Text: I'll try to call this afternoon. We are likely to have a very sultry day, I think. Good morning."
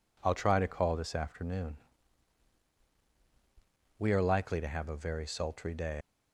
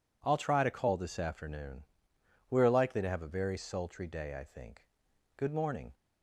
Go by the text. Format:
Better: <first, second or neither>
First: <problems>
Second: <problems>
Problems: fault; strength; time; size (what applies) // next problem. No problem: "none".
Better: second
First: stops before "I think Good morning"; at 6.0 s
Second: none